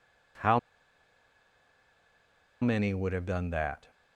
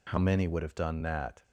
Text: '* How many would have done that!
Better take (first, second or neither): second